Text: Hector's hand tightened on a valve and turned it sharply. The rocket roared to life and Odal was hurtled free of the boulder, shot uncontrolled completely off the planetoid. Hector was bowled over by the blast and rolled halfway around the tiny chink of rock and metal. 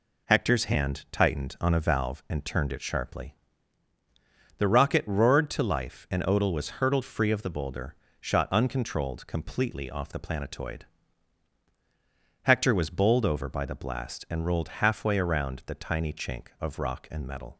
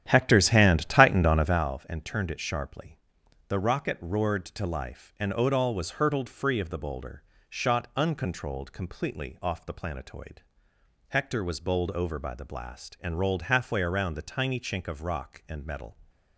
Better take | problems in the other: first | starts louder than the rest; strong; until 1.7 s; 10.5 dB

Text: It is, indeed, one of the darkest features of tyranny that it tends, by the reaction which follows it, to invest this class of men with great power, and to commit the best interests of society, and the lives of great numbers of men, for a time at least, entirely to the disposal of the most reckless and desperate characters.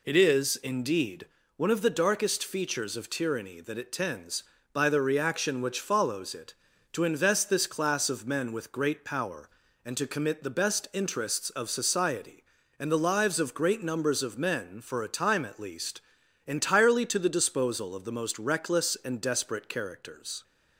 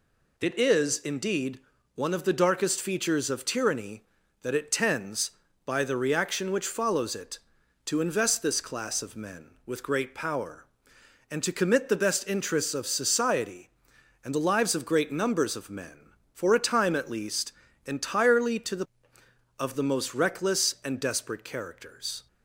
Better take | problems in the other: first | skips "disposal"; at 19.2 s

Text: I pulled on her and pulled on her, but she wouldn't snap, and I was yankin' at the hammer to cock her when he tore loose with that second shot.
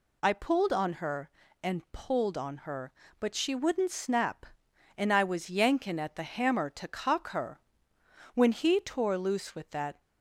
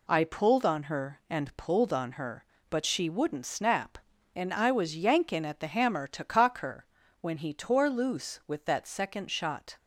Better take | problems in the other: second | pauses between "her" and "when"; noticeable; at 7.5 s; 0.74 s long; slight in the second // stops before "second shot"; at 9.9 s

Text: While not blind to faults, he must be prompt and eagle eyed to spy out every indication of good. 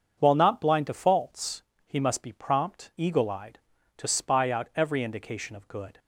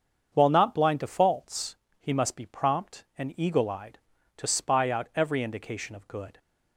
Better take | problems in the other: second | starts louder than the rest; until 1.1 s; 7 dB; strong in the second // skips "and"; at 2.9 s

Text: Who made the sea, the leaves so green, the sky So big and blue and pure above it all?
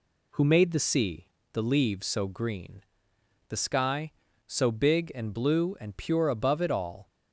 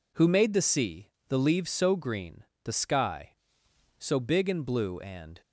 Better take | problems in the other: first | stops before "pure above it all"; at 5.4 s

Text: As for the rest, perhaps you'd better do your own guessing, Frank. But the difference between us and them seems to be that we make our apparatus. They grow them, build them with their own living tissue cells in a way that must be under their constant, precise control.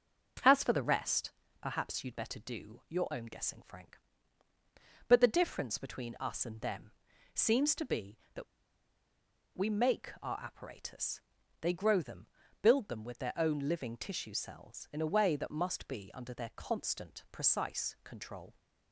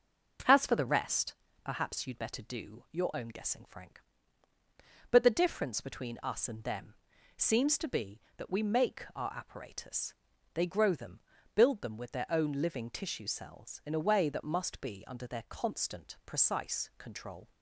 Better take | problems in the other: second | pauses between "them" and "seems"; at 6.9 s; 0.42 s long; also in the second // pauses between "that" and "we"; at 8.4 s; 1.1 s long

